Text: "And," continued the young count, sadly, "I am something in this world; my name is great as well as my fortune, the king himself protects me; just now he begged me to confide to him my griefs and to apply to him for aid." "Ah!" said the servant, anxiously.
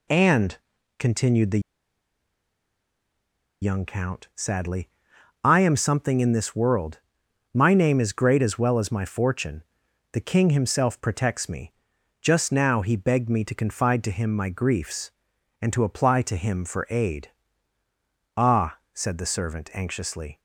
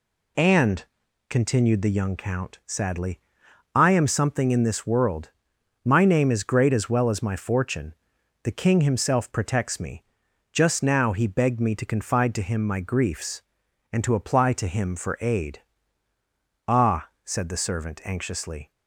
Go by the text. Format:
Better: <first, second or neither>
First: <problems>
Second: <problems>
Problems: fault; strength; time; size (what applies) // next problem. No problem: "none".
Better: second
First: pauses between "the" and "young"; strong; at 1.5 s; 2.0 s long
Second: none